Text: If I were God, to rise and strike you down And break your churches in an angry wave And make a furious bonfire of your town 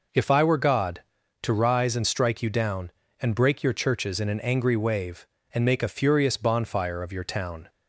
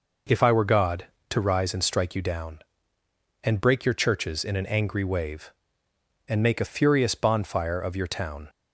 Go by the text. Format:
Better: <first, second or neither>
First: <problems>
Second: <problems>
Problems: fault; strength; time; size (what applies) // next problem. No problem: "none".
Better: neither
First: none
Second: none